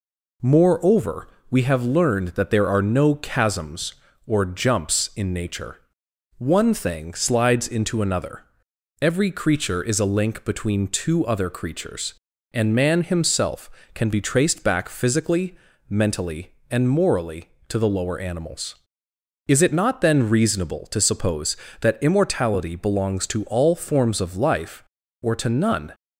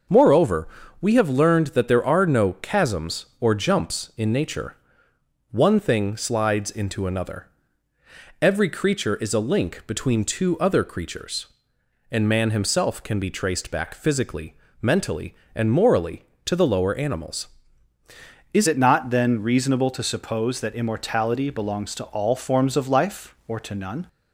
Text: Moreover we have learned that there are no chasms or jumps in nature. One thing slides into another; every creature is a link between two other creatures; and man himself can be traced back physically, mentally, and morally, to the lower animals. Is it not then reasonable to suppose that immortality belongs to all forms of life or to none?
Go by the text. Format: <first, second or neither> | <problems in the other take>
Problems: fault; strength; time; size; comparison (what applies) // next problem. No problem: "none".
first | starts louder than the rest; until 1.4 s; 6 dB // pauses between "Moreover" and "we"; slight; at 0.6 s; 0.32 s long; slight in the first // changes voice at "it"; from 18.6 s on; 5.4 s long